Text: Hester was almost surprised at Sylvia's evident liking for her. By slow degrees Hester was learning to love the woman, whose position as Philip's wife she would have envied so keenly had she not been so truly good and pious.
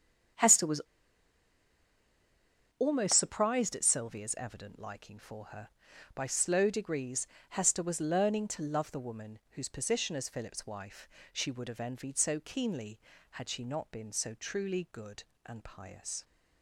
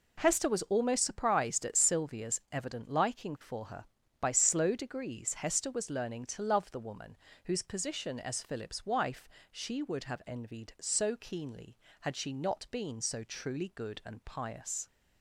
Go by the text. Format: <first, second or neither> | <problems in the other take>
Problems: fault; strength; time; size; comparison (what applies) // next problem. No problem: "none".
second | starts louder than the rest; strong; until 3.3 s; 7.5 dB // pauses between "was" and "almost"; strong; at 0.8 s; 1.9 s long // pauses between "degrees" and "Hester"; slight; at 7.2 s; 0.24 s long // pauses between "wife" and "she"; slight; at 11.0 s; 0.24 s long; slight in the second